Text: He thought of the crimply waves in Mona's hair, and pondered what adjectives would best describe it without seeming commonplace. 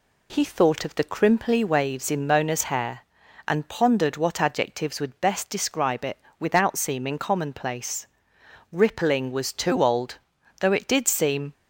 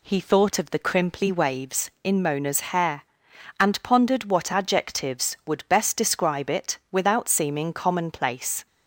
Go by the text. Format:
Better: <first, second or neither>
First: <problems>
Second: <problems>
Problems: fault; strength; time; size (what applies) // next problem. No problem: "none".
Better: second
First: pauses between "it" and "without"; slight; at 6.1 s; 0.22 s long // goes on to say "Rippling was too old though it did seem"; strong; from 8.7 s on; 2.8 s long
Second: pauses between "it" and "without"; slight; at 6.7 s; 0.16 s long